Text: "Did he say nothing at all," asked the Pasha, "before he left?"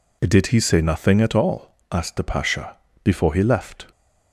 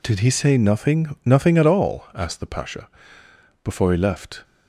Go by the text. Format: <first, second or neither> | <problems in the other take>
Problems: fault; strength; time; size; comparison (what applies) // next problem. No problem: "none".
first | says "nothing" twice; at 1.2 s